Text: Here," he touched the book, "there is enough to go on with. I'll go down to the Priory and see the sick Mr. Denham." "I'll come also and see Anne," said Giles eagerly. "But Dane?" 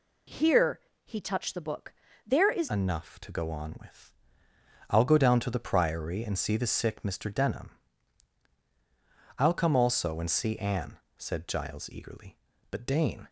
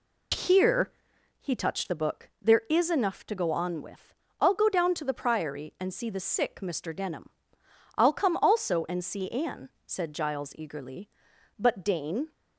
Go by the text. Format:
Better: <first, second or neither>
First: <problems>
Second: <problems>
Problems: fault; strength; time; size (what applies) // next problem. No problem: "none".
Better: second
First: changes voice at "enough"; from 2.6 s on; 10.6 s long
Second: none